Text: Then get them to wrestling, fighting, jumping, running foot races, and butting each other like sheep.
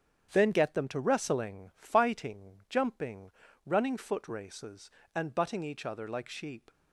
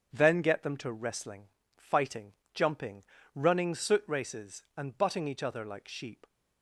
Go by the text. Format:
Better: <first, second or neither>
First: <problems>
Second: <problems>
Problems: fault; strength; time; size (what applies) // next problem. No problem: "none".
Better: first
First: starts louder than the rest; strong; until 1.3 s; 8.5 dB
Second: starts louder than the rest; strong; until 1.1 s; 7.5 dB // says "soot" for "foot"; at 3.7 s